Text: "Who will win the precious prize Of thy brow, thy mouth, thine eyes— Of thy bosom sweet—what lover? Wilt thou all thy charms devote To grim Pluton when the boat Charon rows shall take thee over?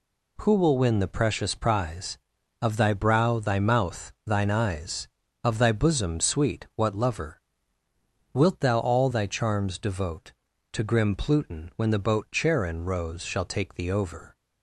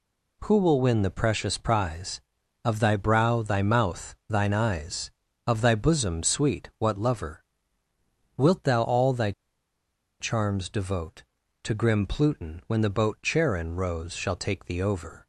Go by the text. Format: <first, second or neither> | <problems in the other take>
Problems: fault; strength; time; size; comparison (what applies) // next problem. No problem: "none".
first | pauses between "thy" and "charms"; noticeable; at 9.3 s; 0.88 s long